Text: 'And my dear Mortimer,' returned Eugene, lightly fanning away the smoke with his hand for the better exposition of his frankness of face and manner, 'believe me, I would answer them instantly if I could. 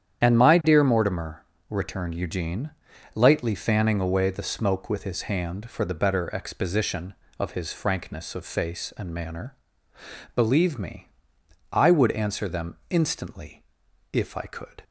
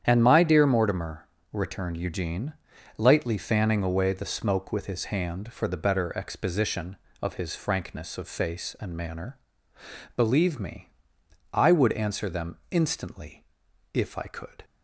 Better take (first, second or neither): second